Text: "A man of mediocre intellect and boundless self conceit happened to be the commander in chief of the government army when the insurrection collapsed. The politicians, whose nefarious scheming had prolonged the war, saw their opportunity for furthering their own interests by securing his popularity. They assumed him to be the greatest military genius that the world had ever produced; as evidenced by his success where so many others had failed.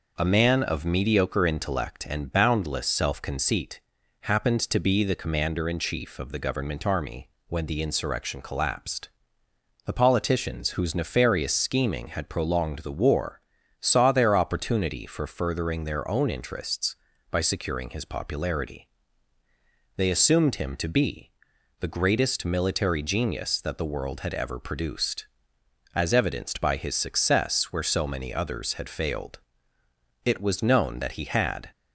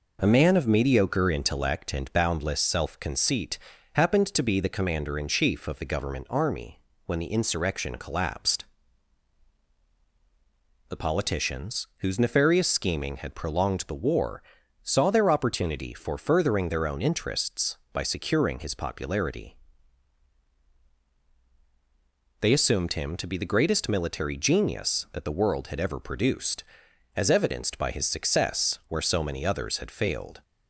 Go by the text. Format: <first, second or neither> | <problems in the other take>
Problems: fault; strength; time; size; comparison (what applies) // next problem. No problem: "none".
second | pauses between "conceit" and "happened"; at 3.8 s; 0.40 s long; slight in the second // pauses between "army" and "when"; slight; at 7.2 s; 0.20 s long; slight in the second // pauses between "be" and "the"; noticeable; at 21.3 s; 0.48 s long // goes on to say "It was known that he had"; from 30.2 s on; 1.4 s long